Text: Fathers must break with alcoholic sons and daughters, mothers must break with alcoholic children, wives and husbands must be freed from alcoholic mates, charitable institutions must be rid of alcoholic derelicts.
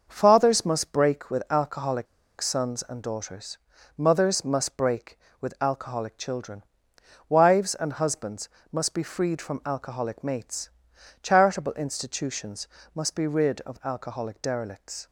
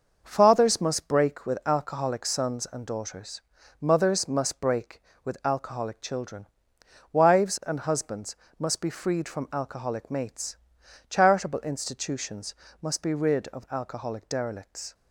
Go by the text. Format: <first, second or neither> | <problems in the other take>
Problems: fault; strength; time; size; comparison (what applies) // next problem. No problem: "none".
second | starts louder than the rest; noticeable; until 1.0 s; 6 dB; also in the second // pauses between "alcoholic" and "sons"; slight; at 2.0 s; 0.34 s long // pauses between "husbands" and "must"; slight; at 8.4 s; 0.24 s long; slight in the second // pauses between "institutions" and "must"; slight; at 12.6 s; 0.28 s long; slight in the second